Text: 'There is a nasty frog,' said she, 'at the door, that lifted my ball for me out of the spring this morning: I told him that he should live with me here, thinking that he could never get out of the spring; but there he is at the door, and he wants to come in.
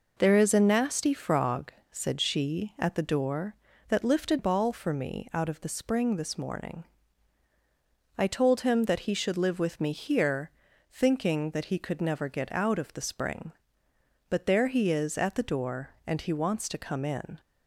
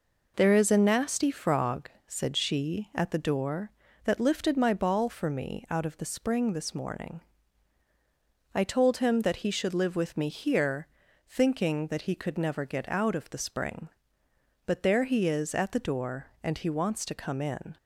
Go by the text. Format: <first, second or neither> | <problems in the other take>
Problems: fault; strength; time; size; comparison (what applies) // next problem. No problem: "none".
second | skips "my"; at 4.3 s